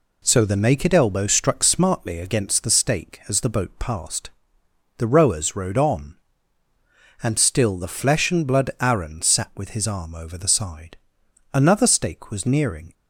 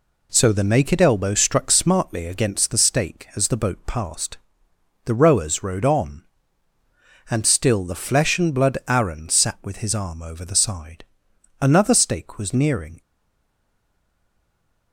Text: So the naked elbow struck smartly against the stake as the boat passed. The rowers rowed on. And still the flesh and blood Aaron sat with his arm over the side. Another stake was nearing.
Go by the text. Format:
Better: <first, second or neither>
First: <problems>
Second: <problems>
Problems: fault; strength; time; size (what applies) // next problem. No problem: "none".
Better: first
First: none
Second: stays silent after the last word; noticeable; from 13.0 s on; 1.9 s long